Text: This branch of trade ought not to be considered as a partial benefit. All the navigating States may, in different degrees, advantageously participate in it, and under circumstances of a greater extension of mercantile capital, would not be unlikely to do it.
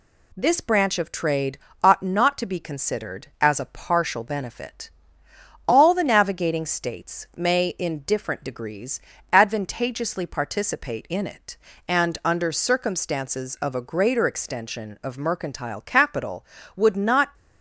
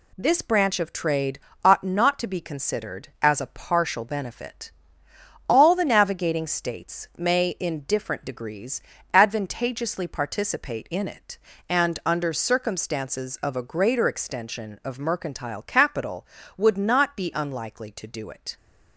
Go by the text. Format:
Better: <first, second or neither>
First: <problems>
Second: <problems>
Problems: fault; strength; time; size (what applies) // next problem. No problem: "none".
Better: second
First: pauses between "trade" and "ought"; slight; at 1.5 s; 0.24 s long // stops before "be unlikely to do it"; at 17.3 s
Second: pauses between "trade" and "ought"; slight; at 1.3 s; 0.24 s long